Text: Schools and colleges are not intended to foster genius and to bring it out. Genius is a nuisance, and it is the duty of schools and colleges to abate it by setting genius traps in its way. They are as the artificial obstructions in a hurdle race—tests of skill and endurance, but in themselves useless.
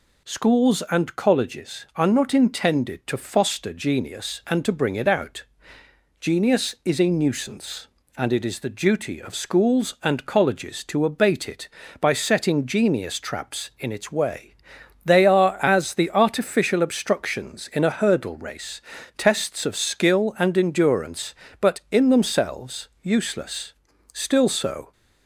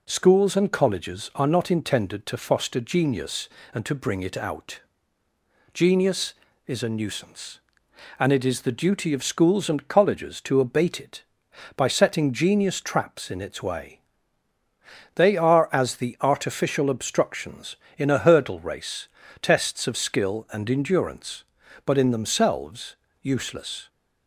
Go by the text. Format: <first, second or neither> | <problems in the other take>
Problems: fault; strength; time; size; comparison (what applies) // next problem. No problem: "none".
second | pauses between "themselves" and "useless"; slight; at 22.8 s; 0.16 s long; slight in the second // goes on to say "Still so"; noticeable; from 24.1 s on; 0.78 s long